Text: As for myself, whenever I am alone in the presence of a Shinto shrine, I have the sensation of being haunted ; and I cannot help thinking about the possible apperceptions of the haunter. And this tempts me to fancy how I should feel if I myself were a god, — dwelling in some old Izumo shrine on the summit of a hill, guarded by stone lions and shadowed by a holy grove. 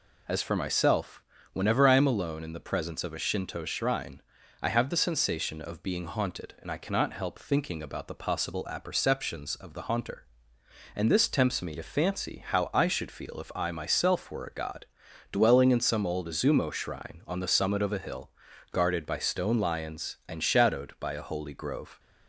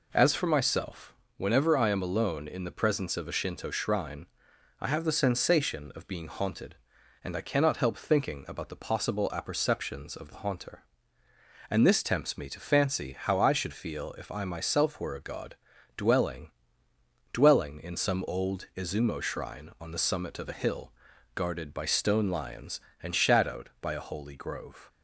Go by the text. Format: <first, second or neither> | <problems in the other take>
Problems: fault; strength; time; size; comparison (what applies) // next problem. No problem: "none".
first | says "dwelling" twice; at 17.3 s